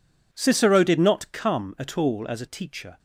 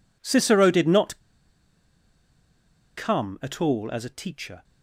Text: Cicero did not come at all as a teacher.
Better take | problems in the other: first | pauses between "not" and "come"; strong; at 1.1 s; 1.7 s long

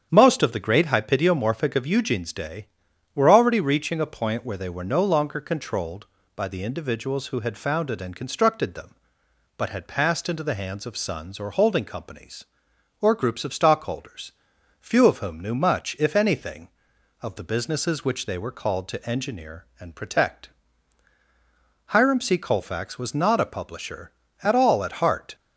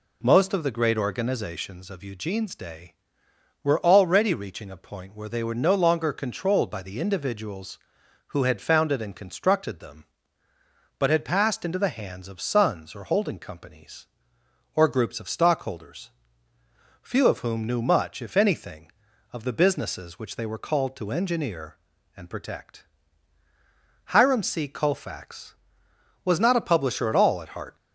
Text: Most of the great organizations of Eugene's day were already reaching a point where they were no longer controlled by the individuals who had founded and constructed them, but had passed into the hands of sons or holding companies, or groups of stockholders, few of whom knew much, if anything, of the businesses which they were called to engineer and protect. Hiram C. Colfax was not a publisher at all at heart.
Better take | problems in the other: second | starts louder than the rest; strong; until 1.1 s; 8.5 dB // says "hypidiomorphic" for "organizations"; at 0.8 s

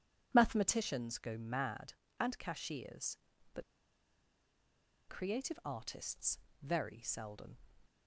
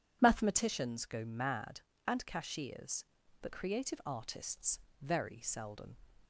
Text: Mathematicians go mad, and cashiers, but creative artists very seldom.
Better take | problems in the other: second | pauses between "but" and "creative"; strong; at 3.6 s; 1.4 s long // pauses between "artists" and "very"; slight; at 6.3 s; 0.20 s long; slight in the second

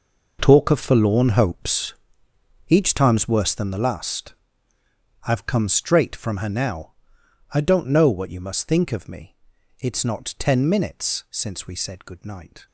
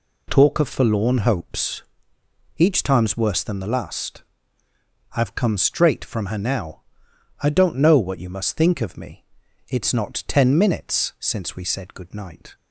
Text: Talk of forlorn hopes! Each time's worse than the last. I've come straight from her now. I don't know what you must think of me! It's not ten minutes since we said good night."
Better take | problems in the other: second | gets quieter; strong; throughout; 14.5 dB

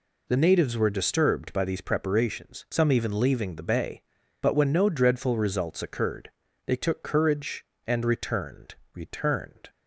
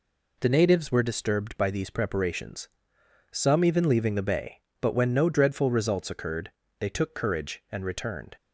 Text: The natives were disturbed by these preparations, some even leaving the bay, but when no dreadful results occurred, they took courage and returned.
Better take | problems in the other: second | says "returned" twice; at 8.9 s

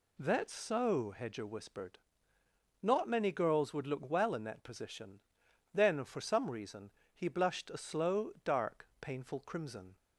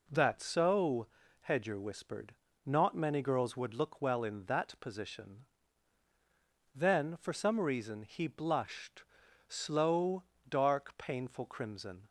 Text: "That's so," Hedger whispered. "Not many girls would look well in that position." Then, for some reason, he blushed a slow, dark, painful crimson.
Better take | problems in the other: first | skips "a"; at 9.2 s

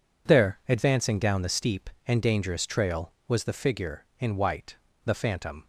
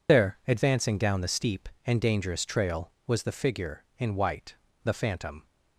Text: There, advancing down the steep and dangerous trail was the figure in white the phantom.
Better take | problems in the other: first | loses the start of "There"; at 0.0 s; 55 ms // pauses between "white" and "the"; slight; at 4.5 s; 0.30 s long; slight in the first

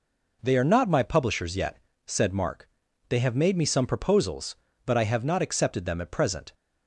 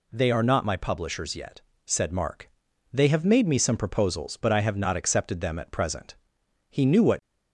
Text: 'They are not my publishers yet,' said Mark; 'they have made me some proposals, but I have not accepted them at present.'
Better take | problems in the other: first | goes on to say "He knew what"; from 6.7 s on; 0.50 s long

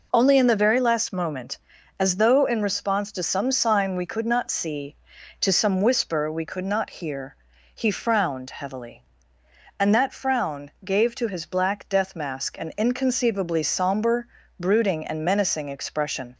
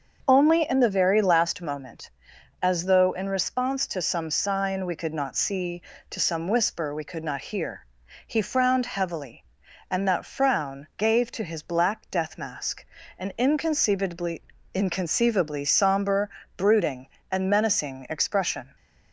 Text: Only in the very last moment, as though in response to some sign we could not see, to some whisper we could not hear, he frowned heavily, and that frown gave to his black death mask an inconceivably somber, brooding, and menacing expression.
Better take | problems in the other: first | starts louder than the rest; until 1.2 s; 6.5 dB // pauses between "mask" and "an"; slight; at 12.8 s; 0.32 s long // says "inconceivably" twice; at 14.7 s

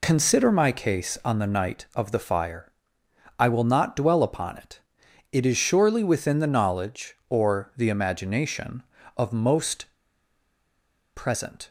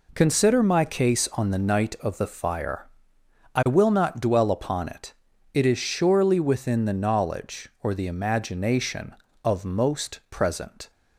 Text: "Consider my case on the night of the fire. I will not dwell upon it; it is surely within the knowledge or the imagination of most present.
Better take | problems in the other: second | pauses between "most" and "present"; strong; at 9.8 s; 1.2 s long

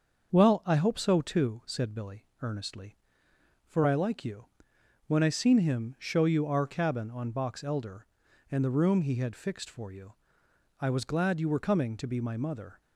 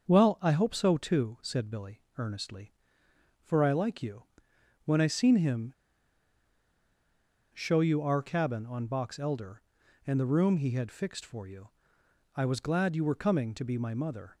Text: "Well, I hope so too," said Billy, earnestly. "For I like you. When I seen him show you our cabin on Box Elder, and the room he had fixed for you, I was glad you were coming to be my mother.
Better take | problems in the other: first | starts louder than the rest; until 1.1 s; 6.5 dB; also in the first // pauses between "him" and "show"; strong; at 5.7 s; 1.7 s long

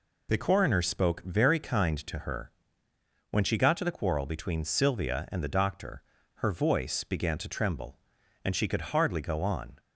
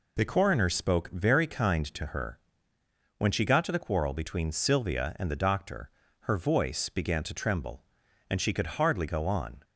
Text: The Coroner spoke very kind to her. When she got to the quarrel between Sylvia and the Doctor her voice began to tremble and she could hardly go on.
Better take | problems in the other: neither | pauses between "Doctor" and "her"; slight; the same in both

